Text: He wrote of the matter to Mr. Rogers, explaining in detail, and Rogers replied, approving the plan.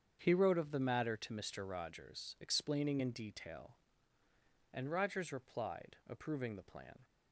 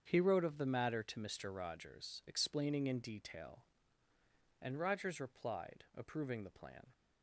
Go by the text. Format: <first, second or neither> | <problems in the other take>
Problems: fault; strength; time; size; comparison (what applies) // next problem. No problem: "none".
neither | starts louder than the rest; strong; the same in both